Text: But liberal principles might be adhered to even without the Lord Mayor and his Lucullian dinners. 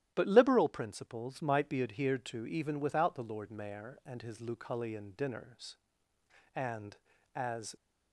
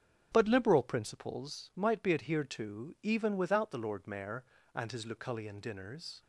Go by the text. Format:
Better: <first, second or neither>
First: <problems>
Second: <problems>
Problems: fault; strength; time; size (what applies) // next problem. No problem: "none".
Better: second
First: starts louder than the rest; strong; until 1.1 s; 12.5 dB // goes on to say "And as"; noticeable; from 6.5 s on; 1.2 s long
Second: starts louder than the rest; strong; until 1.3 s; 7.5 dB